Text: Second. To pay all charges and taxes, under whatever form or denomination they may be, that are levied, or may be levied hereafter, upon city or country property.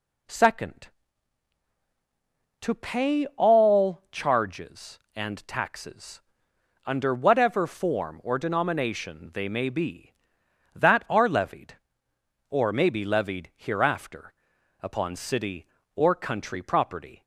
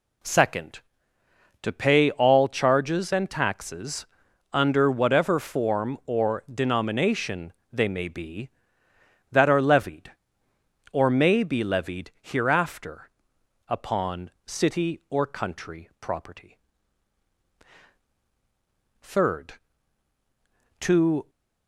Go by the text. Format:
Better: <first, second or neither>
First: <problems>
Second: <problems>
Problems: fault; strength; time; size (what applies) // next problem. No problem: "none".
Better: first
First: none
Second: pauses between "denomination" and "they"; slight; at 7.5 s; 0.18 s long // goes on to say "Third To"; strong; from 19.0 s on; 2.2 s long